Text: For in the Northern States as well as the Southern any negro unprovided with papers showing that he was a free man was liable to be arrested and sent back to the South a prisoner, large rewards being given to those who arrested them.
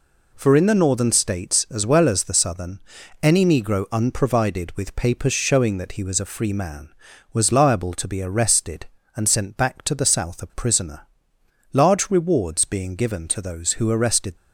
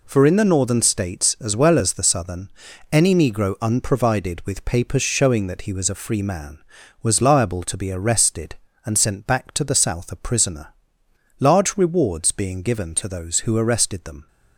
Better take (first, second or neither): second